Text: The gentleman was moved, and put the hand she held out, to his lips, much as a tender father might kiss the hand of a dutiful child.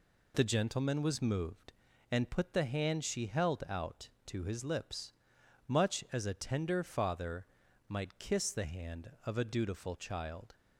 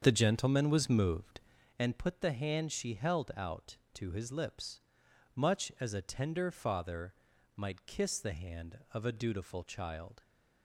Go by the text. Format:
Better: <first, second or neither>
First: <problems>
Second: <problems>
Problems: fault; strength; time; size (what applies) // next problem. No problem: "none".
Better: first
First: pauses between "father" and "might"; at 7.4 s; 0.42 s long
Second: starts louder than the rest; strong; until 1.8 s; 7.5 dB // pauses between "father" and "might"; at 7.1 s; 0.42 s long